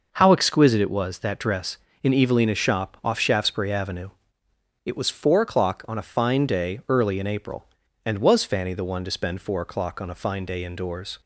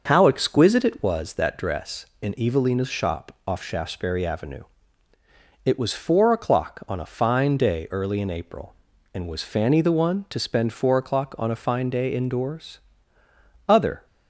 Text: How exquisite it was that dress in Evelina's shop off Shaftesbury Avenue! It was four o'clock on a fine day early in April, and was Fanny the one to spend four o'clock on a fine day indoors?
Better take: first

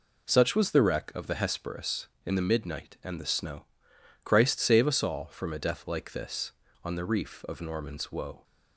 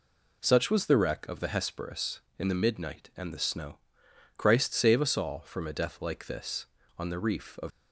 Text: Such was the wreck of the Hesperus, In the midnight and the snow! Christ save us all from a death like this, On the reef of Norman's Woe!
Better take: first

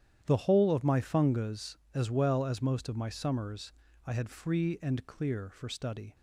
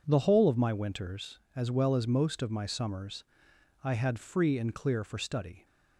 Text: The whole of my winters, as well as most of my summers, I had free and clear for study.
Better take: second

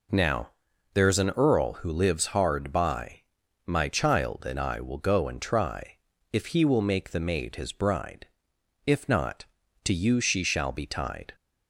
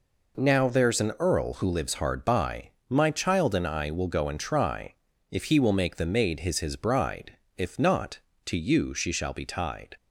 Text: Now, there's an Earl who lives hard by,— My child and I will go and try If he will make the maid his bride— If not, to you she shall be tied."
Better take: first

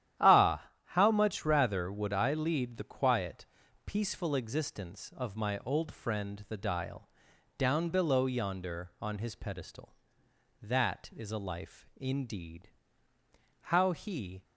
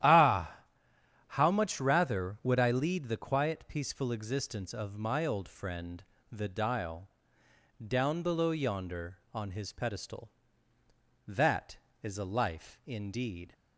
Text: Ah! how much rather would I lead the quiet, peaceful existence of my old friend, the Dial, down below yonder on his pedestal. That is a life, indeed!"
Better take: second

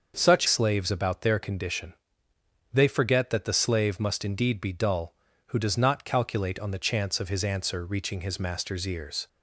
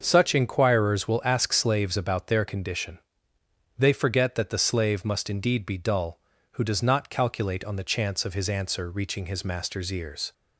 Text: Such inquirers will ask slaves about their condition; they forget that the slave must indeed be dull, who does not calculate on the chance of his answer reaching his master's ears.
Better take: second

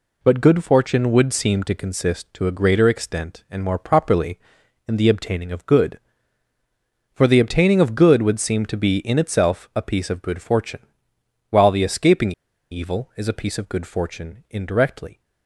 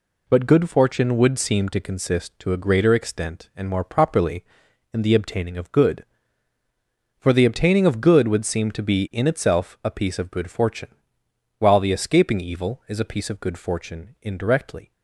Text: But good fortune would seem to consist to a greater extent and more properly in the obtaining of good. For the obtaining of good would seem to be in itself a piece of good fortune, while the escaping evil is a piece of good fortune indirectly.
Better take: second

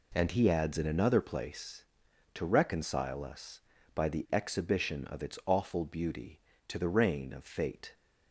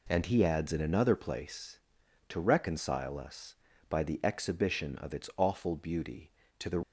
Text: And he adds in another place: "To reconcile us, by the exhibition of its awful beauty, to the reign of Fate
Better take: first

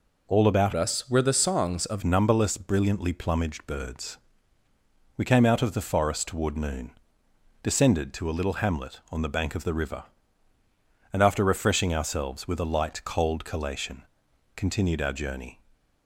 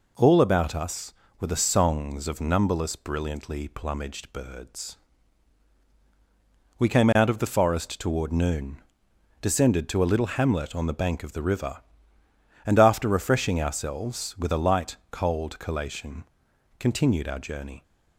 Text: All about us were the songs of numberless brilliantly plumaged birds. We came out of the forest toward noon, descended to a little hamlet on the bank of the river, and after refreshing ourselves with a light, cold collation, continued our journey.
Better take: second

